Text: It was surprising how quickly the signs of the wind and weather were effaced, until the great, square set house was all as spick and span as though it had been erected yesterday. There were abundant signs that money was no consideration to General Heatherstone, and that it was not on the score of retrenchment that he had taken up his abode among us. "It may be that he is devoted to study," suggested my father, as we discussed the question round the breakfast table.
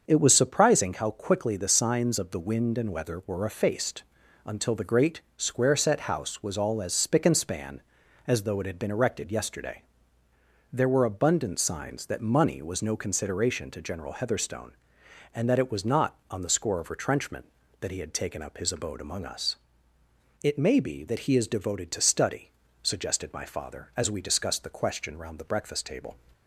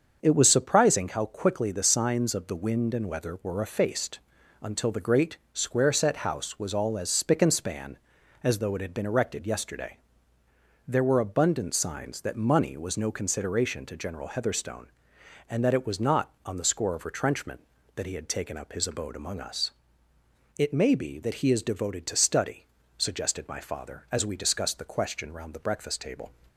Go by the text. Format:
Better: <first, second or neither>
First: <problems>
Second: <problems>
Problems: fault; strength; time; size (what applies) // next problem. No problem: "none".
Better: neither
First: starts louder than the rest; until 1.0 s; 6.5 dB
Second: starts louder than the rest; until 1.2 s; 6.5 dB